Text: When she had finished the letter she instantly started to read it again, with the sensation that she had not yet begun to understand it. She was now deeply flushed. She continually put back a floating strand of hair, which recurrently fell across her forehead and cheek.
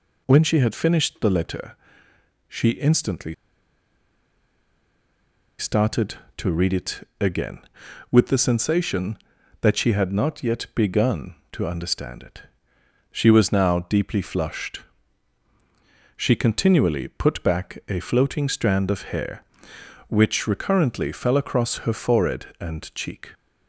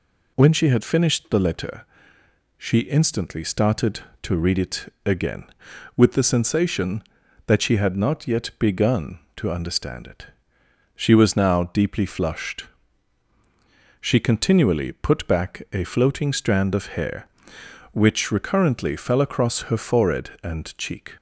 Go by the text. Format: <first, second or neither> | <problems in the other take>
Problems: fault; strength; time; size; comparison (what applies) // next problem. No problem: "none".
second | pauses between "letter" and "she"; noticeable; at 1.7 s; 0.72 s long; noticeable in the second // pauses between "instantly" and "started"; strong; at 3.3 s; 2.2 s long